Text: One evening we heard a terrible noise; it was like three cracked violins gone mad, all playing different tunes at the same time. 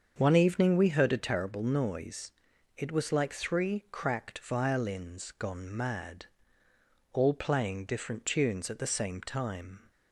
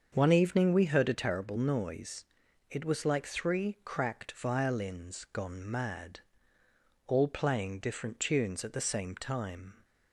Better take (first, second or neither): neither